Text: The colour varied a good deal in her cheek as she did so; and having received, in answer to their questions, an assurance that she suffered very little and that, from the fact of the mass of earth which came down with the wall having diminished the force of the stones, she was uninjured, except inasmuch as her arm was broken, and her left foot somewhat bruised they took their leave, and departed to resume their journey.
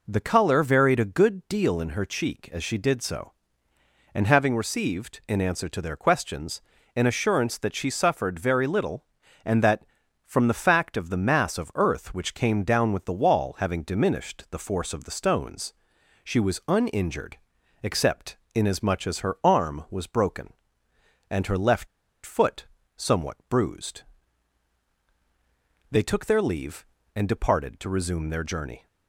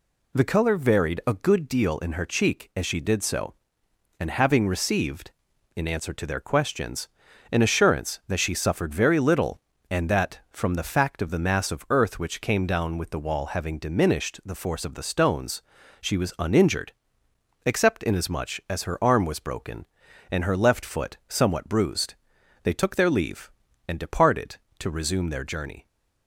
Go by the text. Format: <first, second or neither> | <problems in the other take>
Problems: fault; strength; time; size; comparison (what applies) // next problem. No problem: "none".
second | pauses between "except" and "inasmuch"; slight; at 18.3 s; 0.18 s long // pauses between "left" and "foot"; at 21.8 s; 0.39 s long // pauses between "foot" and "somewhat"; slight; at 22.6 s; 0.30 s long // pauses between "bruised" and "they"; strong; at 24.0 s; 1.8 s long; noticeable in the second